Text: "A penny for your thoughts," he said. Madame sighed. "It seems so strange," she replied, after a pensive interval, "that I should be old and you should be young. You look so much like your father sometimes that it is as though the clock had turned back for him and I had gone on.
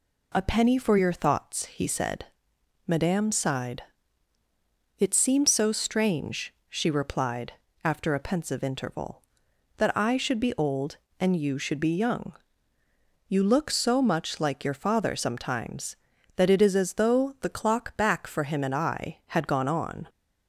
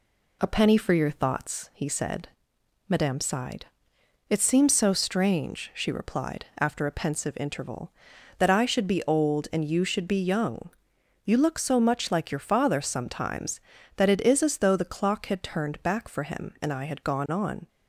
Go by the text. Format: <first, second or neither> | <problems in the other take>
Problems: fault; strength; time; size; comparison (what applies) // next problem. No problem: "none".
second | skips "had turned"; at 17.9 s